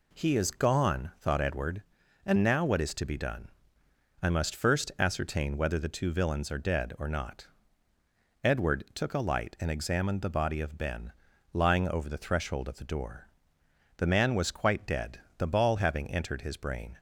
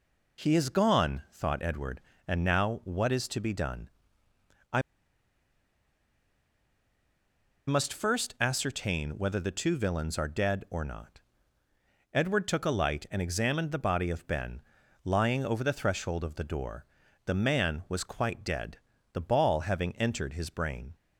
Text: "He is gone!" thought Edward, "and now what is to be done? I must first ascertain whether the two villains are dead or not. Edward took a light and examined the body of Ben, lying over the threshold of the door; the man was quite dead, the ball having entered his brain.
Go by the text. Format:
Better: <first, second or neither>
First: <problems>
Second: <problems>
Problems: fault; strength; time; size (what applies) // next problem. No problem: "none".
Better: first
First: none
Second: pauses between "I" and "must"; strong; at 4.8 s; 2.8 s long